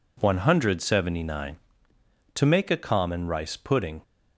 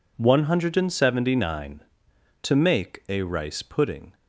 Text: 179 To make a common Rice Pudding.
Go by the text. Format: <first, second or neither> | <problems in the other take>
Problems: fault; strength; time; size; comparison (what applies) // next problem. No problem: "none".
first | skips "common"; at 3.2 s